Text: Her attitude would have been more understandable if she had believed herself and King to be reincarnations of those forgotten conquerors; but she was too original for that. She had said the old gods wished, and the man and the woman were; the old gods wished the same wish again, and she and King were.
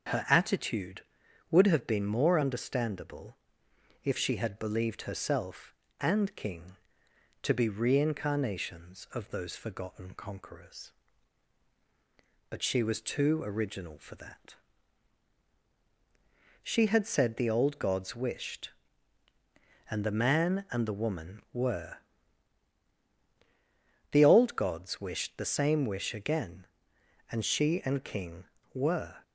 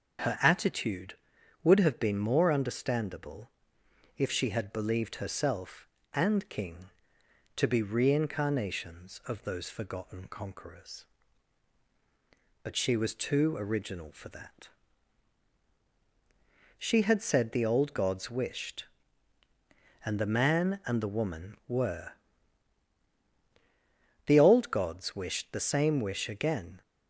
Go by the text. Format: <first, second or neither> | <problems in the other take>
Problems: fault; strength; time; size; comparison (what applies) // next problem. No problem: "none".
first | starts louder than the rest; strong; until 1.7 s; 7.5 dB; strong in the first // pauses between "understandable" and "if"; noticeable; at 3.4 s; 0.70 s long; noticeable in the first // stops before "and she and King were"; at 26.8 s